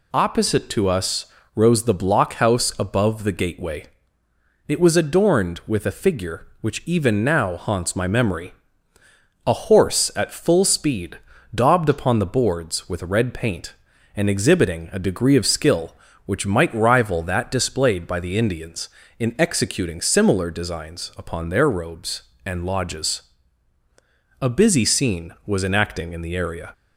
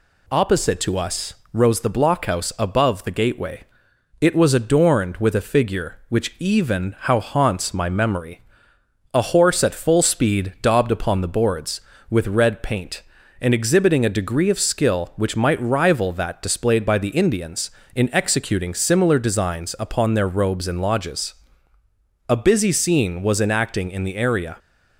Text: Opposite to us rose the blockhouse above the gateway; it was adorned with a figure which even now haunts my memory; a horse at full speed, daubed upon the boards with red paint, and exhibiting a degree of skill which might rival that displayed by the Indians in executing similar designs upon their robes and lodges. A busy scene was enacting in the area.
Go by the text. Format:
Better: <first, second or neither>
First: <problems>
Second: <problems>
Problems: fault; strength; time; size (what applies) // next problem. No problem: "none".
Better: first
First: pauses between "us" and "rose"; slight; at 1.2 s; 0.28 s long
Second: pauses between "us" and "rose"; slight; at 1.3 s; 0.18 s long // says "how" for "now"; at 6.9 s